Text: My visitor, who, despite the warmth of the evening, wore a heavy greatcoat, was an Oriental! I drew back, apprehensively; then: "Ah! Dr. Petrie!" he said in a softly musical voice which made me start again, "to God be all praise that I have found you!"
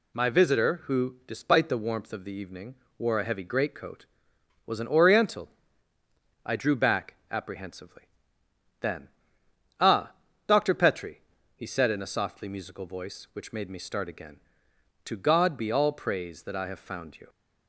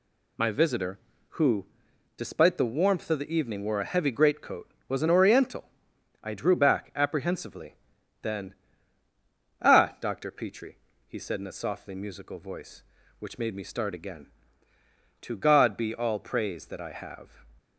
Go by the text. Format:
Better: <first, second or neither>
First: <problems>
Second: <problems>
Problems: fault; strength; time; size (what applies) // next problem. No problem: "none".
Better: first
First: none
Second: stops before "found you"; at 17.5 s